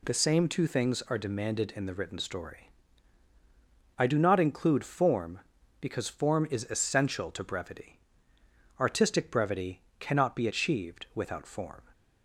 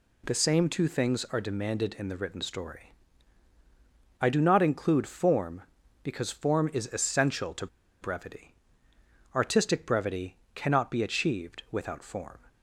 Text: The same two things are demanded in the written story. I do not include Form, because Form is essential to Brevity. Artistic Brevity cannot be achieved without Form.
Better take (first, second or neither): first